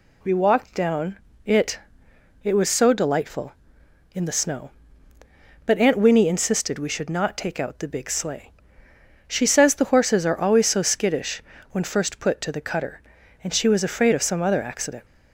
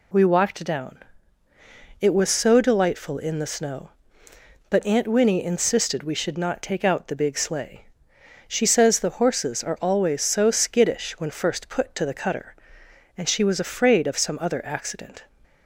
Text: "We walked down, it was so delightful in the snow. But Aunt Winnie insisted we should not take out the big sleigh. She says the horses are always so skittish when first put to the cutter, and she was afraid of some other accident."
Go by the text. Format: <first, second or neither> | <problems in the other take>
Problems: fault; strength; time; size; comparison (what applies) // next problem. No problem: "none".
second | says "it" twice; at 2.4 s // pauses between "skittish" and "when"; slight; at 11.4 s; 0.30 s long